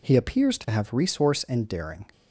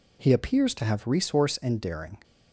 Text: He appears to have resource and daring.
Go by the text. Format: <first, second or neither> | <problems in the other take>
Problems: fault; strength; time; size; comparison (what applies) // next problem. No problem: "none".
neither | none